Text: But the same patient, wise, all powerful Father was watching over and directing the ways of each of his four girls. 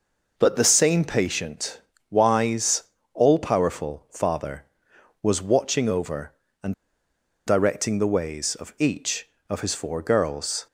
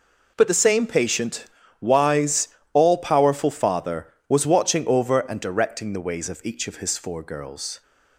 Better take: second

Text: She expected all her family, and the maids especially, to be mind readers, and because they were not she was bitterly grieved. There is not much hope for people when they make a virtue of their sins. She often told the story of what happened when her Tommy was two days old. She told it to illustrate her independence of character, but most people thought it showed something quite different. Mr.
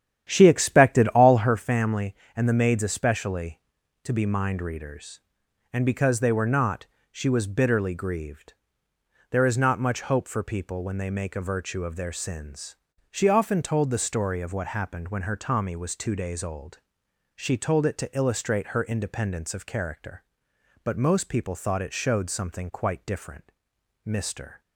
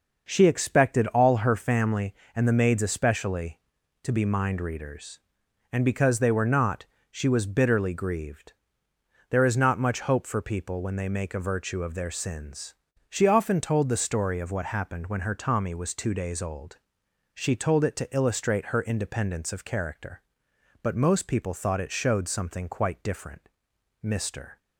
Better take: second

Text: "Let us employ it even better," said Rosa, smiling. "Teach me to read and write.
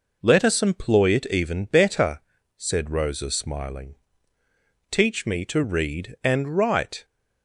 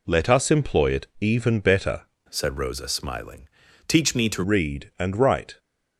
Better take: first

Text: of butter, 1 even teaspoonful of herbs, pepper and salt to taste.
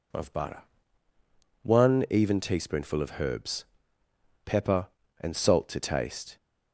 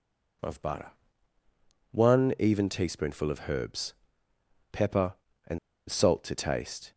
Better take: first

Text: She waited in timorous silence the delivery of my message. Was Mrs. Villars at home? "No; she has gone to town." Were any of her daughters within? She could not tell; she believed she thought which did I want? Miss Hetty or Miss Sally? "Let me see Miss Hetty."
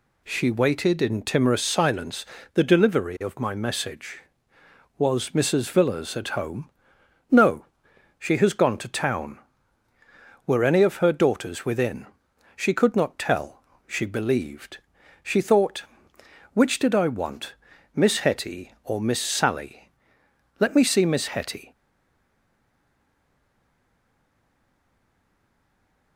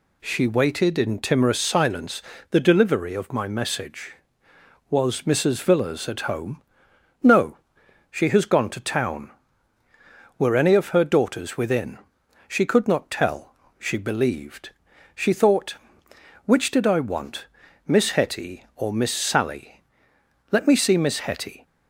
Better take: second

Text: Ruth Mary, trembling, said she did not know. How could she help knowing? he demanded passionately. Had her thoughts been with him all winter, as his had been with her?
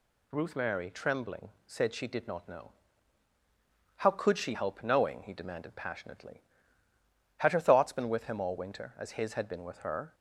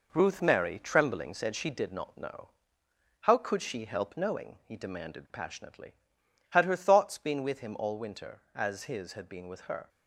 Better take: first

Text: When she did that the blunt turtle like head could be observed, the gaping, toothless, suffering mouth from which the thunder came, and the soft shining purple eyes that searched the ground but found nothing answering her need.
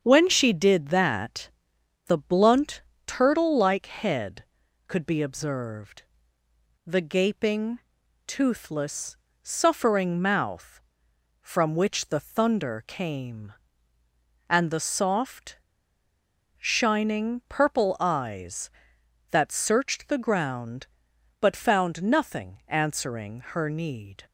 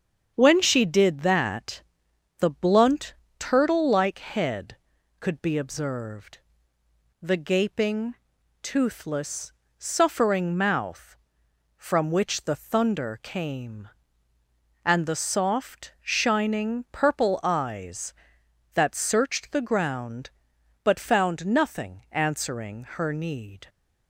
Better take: second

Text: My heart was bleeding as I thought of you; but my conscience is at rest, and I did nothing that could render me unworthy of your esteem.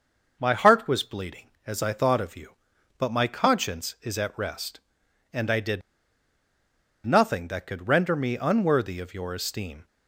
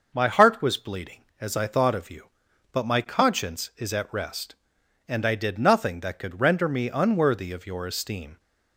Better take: second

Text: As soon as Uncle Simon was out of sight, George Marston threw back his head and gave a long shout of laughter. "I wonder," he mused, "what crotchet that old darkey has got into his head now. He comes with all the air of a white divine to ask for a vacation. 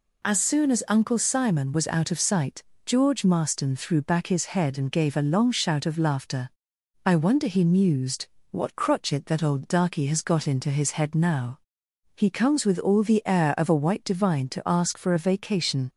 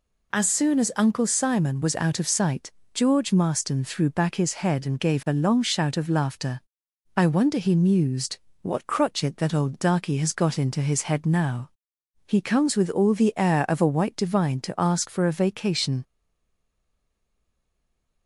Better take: first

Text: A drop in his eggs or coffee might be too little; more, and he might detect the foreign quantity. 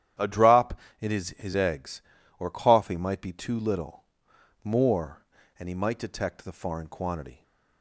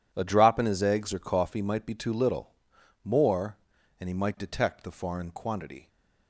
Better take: second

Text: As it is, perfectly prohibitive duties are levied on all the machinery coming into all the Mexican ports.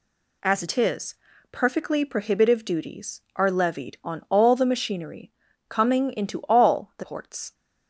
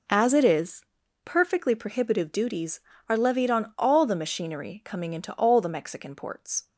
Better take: second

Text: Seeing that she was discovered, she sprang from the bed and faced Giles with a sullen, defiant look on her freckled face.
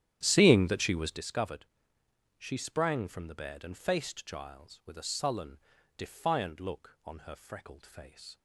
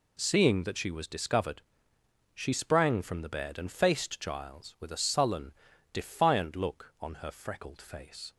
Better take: second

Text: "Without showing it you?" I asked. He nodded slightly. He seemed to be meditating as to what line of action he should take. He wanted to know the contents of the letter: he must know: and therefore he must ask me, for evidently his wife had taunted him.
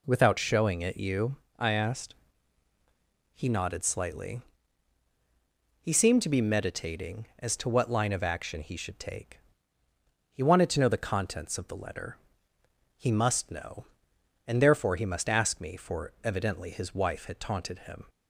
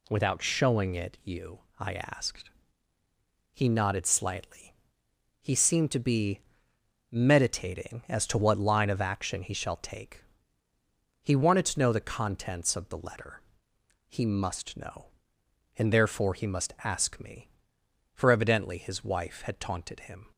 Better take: first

